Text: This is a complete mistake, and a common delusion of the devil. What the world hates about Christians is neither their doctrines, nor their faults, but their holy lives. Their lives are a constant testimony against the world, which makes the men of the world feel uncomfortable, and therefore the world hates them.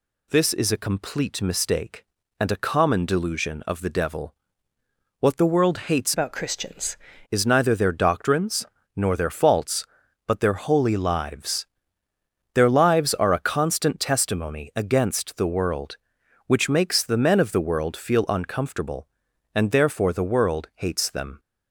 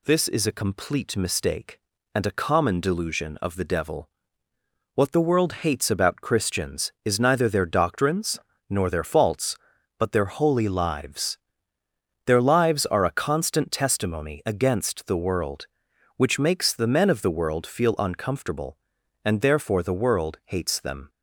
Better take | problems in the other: second | changes voice from "about" to "Christians"; from 6.1 to 6.9 s; 0.8 s long

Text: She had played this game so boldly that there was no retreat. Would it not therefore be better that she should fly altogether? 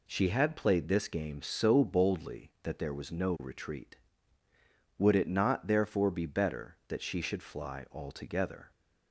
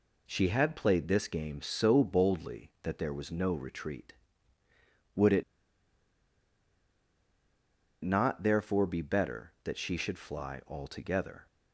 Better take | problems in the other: first | pauses between "it" and "not"; strong; at 5.4 s; 2.6 s long

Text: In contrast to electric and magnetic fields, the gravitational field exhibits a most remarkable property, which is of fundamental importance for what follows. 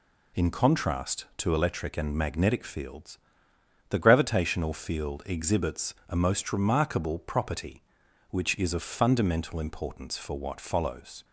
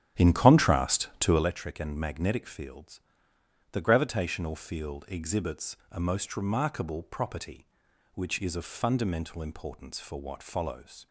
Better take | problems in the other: first | starts louder than the rest; strong; until 1.5 s; 11 dB // pauses between "exhibits" and "a"; slight; at 5.7 s; 0.16 s long; slight in the first

